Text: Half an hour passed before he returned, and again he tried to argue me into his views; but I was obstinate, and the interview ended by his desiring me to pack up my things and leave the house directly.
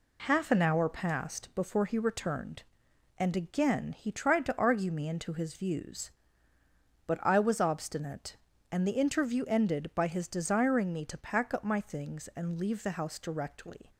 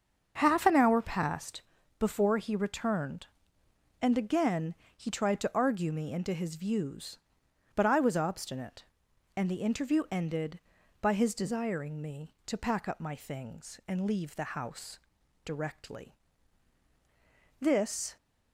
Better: first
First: none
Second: starts louder than the rest; until 1.4 s; 7 dB // pauses between "passed" and "before"; slight; at 1.6 s; 0.36 s long // pauses between "again" and "he"; slight; at 4.7 s; 0.20 s long // pauses between "house" and "directly"; noticeable; at 14.9 s; 0.48 s long // goes on to say "This"; from 17.5 s on; 0.58 s long

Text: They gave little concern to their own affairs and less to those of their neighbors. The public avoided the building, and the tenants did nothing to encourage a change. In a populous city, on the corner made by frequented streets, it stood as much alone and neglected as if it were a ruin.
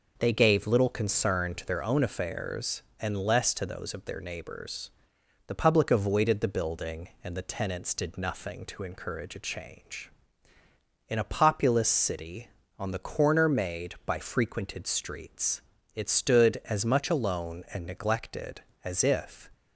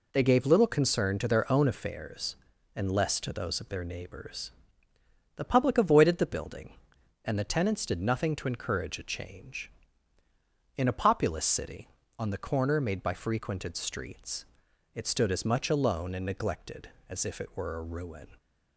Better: second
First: stops before "it were a ruin"; at 19.5 s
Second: none

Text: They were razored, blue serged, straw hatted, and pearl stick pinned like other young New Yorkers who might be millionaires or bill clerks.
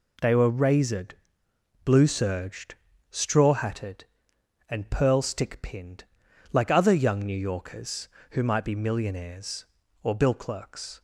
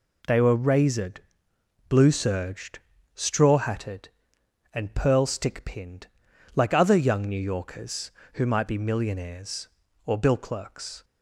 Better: neither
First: pauses between "pinned" and "like"; noticeable; at 6.0 s; 0.48 s long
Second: pauses between "pinned" and "like"; noticeable; at 6.0 s; 0.48 s long

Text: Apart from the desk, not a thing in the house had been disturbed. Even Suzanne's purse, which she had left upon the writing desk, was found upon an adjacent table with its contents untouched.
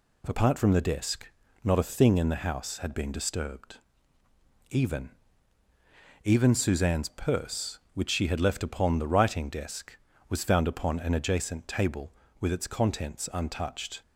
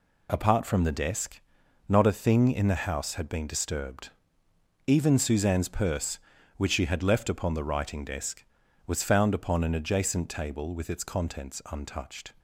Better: second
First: says "Even" twice; at 6.2 s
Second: none

